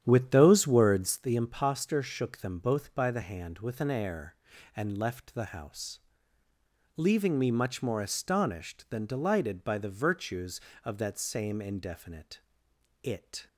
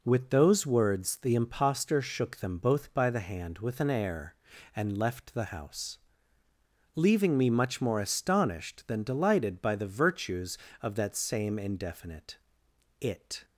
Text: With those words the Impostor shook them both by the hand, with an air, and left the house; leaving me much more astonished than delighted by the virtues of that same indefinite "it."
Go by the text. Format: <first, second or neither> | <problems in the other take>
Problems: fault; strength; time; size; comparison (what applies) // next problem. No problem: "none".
second | starts louder than the rest; strong; until 1.3 s; 9.5 dB // pauses between "indefinite" and "it"; noticeable; at 12.4 s; 0.62 s long; noticeable in the second